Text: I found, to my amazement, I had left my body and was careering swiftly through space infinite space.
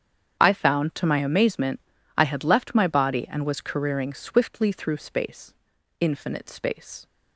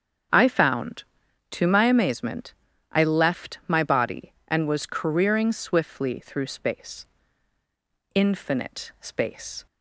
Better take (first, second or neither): first